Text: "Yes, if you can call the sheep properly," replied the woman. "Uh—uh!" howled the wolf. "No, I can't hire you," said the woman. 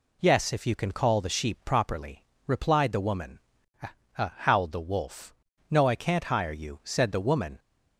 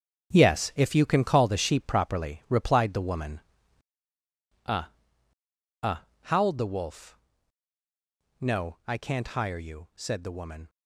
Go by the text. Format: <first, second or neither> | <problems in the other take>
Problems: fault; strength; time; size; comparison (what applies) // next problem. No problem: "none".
first | gets quieter; strong; throughout; 11.5 dB